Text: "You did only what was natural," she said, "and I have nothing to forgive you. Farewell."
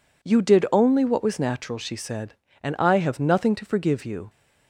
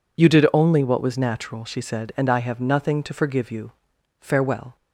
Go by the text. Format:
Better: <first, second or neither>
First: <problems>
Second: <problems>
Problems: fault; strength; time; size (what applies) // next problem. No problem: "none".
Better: second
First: stops before "Farewell"; at 4.2 s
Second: none